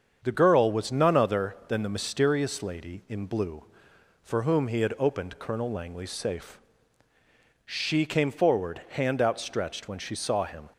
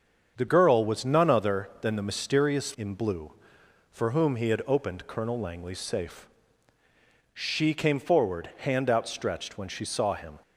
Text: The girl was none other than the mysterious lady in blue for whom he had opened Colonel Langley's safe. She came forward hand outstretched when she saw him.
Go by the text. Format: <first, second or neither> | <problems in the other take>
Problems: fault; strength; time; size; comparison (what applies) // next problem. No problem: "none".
first | starts louder than the rest; until 1.4 s; 7 dB; strong in the first // skips "lady"; at 2.7 s